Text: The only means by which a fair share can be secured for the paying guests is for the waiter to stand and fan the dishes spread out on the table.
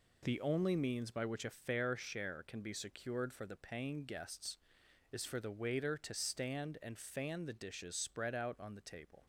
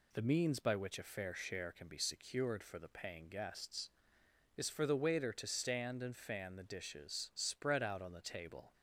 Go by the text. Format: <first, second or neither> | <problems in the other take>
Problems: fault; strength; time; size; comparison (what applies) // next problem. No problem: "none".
first | skips "only"; at 0.2 s